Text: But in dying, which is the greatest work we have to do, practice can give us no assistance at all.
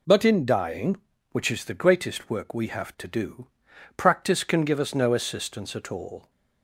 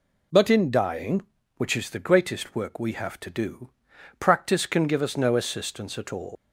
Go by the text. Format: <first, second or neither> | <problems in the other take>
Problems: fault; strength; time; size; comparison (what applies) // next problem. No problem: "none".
first | leaves "all" unfinished; at 6.3 s; 155 ms